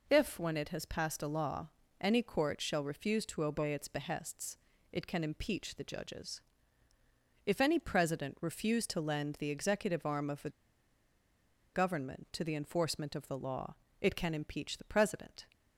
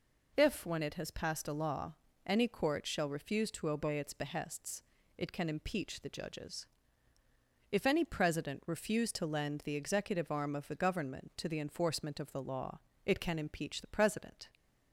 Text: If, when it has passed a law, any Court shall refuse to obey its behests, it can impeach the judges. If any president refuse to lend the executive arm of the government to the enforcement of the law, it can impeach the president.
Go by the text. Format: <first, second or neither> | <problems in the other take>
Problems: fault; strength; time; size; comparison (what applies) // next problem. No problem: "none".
second | pauses between "the" and "government"; at 10.4 s; 1.2 s long